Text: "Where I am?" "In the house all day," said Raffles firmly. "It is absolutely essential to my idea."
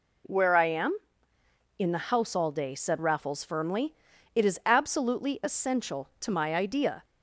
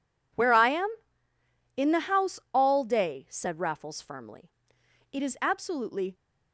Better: first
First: none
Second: pauses between "house" and "all"; slight; at 2.3 s; 0.16 s long // stops before "essential to my idea"; at 6.1 s

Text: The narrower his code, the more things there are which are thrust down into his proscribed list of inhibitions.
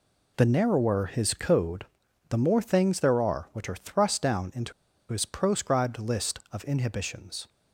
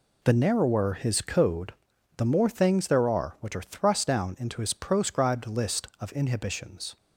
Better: second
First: pauses between "into" and "his"; at 4.7 s; 0.38 s long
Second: none

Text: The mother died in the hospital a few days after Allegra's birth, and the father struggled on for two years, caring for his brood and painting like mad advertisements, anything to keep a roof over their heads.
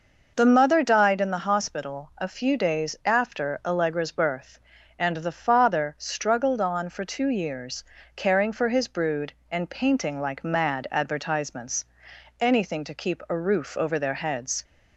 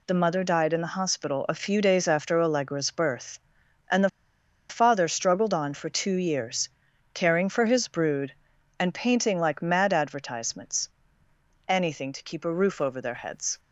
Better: first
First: none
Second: pauses between "the" and "father"; noticeable; at 4.0 s; 0.60 s long

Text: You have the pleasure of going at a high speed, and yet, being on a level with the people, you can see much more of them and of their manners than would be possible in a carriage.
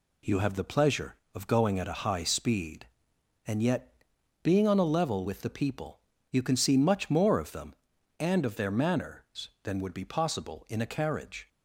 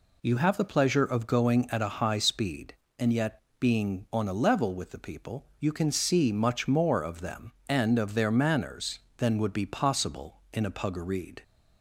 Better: first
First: none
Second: says "puggareed" for "carriage"; at 10.7 s

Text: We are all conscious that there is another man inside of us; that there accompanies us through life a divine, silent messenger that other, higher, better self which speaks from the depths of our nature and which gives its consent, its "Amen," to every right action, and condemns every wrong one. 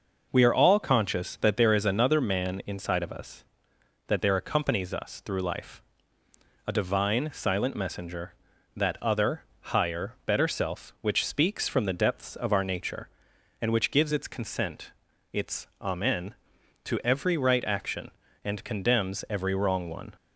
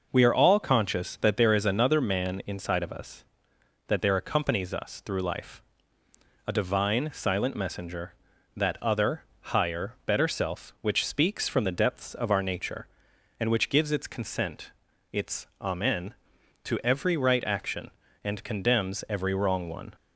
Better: neither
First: pauses between "life" and "a"; noticeable; at 5.8 s; 0.86 s long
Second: pauses between "life" and "a"; noticeable; at 5.6 s; 0.86 s long

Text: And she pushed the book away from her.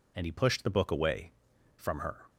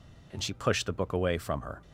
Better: second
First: says "he" for "she"; at 0.2 s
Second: none

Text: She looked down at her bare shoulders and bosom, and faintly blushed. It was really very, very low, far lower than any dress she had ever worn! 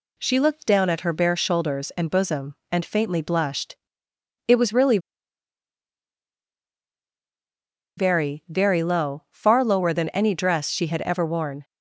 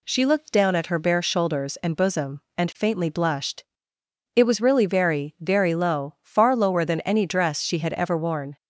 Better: second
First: pauses between "really" and "very"; strong; at 4.9 s; 2.9 s long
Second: none

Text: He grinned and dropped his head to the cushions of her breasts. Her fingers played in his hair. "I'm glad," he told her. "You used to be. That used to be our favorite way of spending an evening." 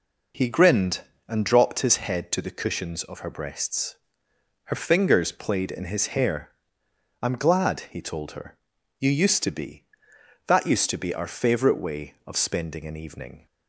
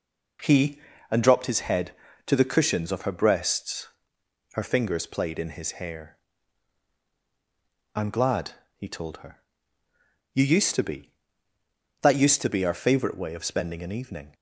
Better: first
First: none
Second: skips "grinned"; at 0.9 s

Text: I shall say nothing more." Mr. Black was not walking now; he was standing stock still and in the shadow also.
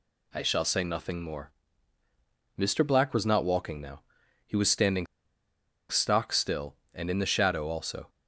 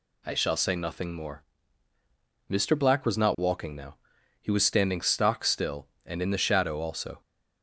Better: second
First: pauses between "standing" and "stock"; noticeable; at 5.0 s; 0.84 s long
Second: none

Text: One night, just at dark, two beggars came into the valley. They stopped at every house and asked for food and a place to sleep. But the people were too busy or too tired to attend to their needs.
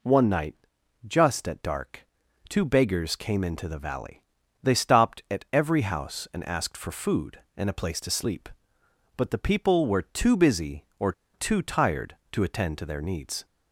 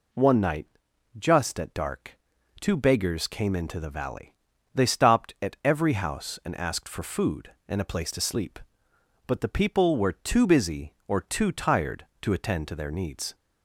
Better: second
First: pauses between "or" and "too"; slight; at 11.1 s; 0.21 s long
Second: none

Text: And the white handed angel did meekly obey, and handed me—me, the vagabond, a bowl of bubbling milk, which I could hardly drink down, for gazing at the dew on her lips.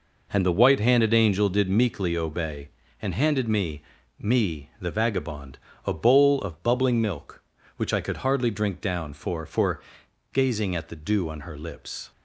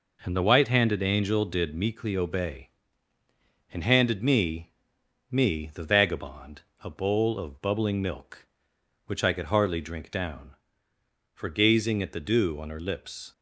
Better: second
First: says "for" twice; at 9.4 s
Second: none

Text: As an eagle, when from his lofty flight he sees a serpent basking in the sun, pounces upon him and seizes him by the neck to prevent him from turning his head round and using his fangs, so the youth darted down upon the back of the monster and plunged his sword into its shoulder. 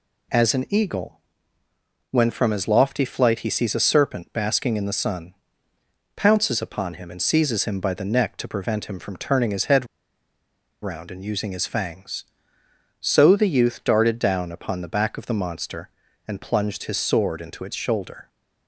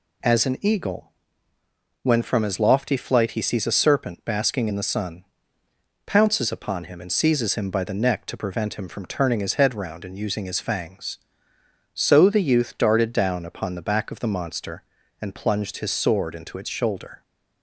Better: second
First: pauses between "head" and "round"; noticeable; at 9.8 s; 0.95 s long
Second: none

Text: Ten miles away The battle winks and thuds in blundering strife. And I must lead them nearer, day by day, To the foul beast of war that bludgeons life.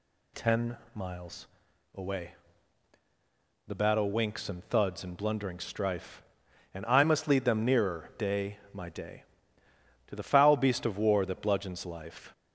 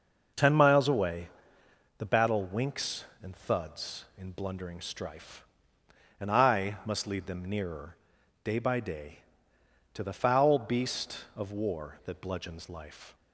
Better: second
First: pauses between "Ten" and "miles"; slight; at 0.7 s; 0.18 s long // pauses between "miles" and "away"; noticeable; at 1.4 s; 0.47 s long // pauses between "away" and "The"; strong; at 2.3 s; 1.3 s long // says "my" for "by"; at 8.7 s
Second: pauses between "away" and "The"; noticeable; at 1.2 s; 0.70 s long

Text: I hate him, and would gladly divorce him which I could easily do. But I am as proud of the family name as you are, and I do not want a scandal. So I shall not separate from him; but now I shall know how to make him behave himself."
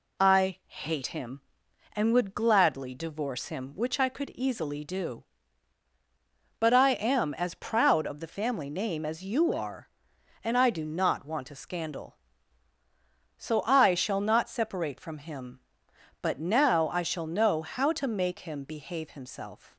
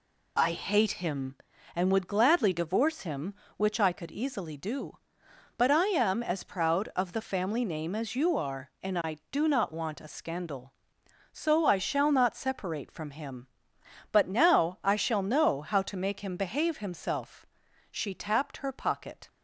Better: first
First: none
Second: goes on to say "She tapped her pocket"; from 17.9 s on; 1.3 s long

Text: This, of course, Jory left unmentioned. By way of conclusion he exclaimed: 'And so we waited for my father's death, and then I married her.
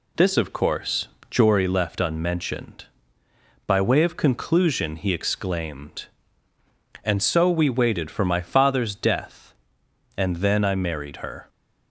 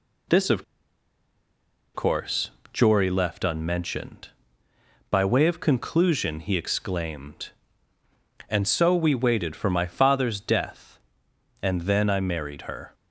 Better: first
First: none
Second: pauses between "of" and "course"; strong; at 0.6 s; 1.3 s long

